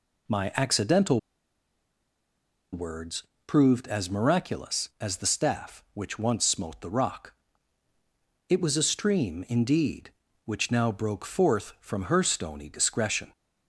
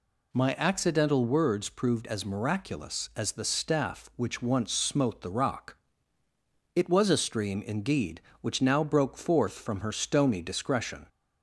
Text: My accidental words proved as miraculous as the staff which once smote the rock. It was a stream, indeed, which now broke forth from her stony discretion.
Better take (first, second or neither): second